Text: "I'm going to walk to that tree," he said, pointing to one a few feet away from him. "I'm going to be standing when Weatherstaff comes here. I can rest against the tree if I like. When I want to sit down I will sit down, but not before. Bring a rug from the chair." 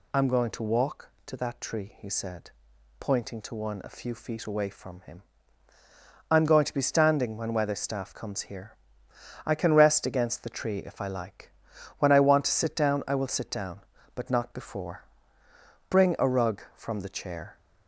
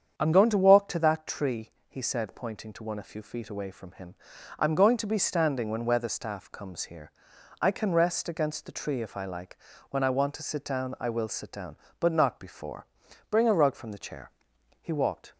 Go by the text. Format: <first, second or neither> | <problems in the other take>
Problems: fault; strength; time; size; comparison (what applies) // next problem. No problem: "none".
first | starts louder than the rest; strong; until 1.2 s; 8 dB // goes on to say "He walked"; from 14.8 s on; 0.52 s long